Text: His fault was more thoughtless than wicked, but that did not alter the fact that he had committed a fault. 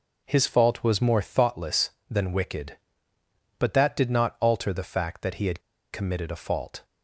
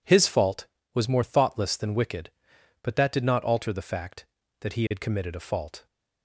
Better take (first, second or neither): second